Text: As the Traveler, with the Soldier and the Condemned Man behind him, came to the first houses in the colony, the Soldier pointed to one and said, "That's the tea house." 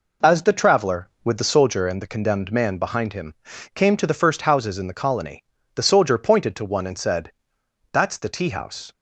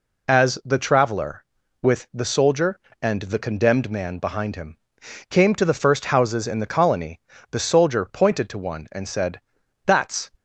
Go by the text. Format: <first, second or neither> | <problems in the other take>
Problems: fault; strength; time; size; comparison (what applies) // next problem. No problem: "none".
first | stops before "the tea house"; at 10.3 s